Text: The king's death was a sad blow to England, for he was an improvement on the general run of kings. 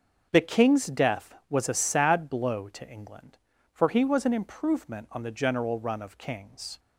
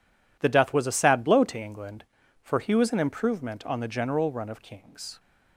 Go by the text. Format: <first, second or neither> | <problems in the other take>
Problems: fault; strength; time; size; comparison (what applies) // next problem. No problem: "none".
first | skips "king's"; at 0.4 s